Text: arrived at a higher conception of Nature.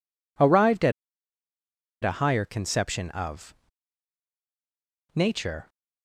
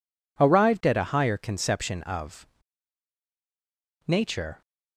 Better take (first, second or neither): second